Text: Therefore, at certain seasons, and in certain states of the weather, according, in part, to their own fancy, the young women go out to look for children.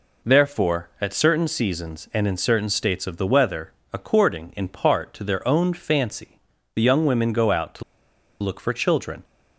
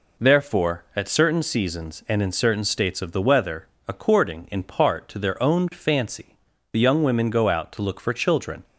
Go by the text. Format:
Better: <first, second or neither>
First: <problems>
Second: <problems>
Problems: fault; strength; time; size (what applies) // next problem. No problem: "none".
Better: second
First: pauses between "to" and "look"; noticeable; at 7.8 s; 0.58 s long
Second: none